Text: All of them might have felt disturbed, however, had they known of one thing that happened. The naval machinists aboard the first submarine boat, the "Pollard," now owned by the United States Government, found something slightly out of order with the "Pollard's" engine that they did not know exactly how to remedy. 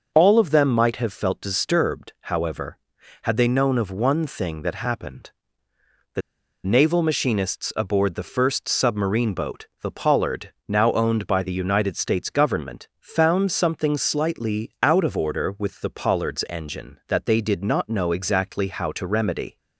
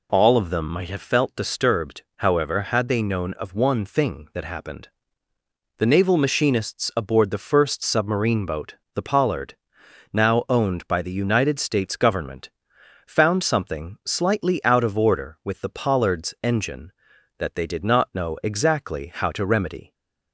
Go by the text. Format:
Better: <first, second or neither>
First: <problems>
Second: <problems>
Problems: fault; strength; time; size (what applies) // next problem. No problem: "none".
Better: second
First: pauses between "The" and "naval"; at 6.2 s; 0.43 s long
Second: none